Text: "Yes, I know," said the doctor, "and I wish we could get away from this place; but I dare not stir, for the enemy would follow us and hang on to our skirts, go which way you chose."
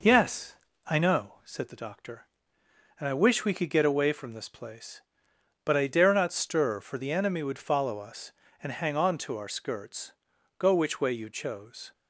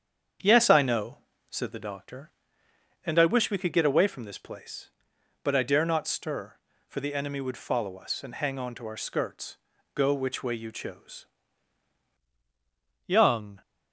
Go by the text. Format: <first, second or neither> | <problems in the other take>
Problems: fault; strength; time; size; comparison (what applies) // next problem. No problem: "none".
first | starts louder than the rest; strong; until 1.7 s; 7 dB // goes on to say "Young"; from 13.0 s on; 0.56 s long